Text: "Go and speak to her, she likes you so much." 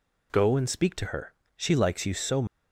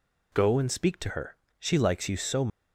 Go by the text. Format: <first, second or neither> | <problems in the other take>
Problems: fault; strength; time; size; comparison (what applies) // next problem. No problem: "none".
neither | none